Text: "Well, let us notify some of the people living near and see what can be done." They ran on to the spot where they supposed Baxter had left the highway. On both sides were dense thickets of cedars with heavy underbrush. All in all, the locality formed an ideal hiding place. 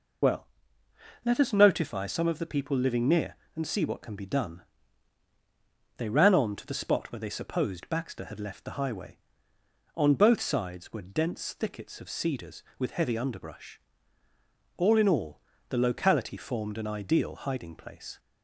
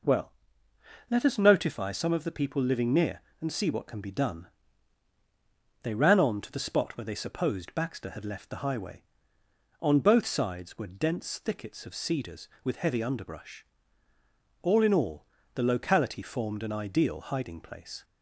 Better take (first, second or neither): second